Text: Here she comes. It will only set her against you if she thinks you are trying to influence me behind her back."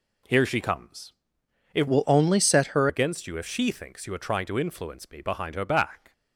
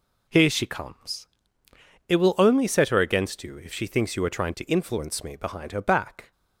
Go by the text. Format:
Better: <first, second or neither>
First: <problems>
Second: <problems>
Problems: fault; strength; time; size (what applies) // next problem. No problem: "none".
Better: second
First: changes voice from "will" to "her"; from 1.8 to 2.8 s; 1.0 s long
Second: none